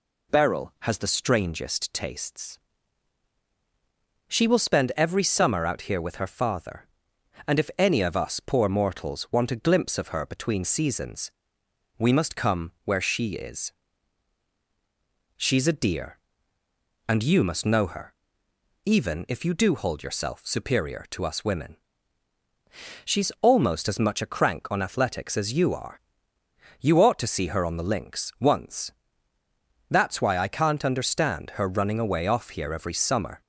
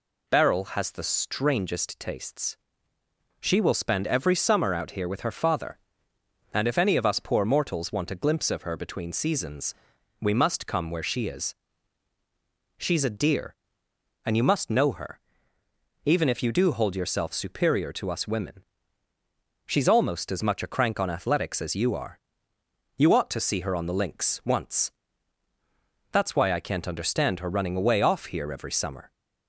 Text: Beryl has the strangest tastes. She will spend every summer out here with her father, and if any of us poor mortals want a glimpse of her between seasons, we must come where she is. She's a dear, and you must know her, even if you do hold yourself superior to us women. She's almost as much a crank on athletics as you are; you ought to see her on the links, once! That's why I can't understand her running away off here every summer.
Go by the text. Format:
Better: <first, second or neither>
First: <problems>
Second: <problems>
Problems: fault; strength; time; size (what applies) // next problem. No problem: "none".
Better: neither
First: none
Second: none